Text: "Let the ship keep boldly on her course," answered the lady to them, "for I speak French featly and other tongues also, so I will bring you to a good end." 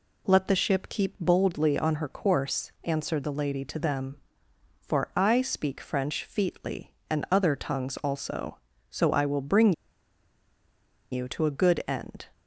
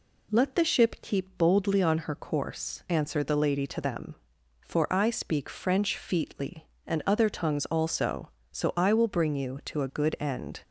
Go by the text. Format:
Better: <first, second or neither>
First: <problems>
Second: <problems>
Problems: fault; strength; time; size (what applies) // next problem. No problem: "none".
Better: second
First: pauses between "bring" and "you"; strong; at 9.7 s; 1.3 s long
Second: none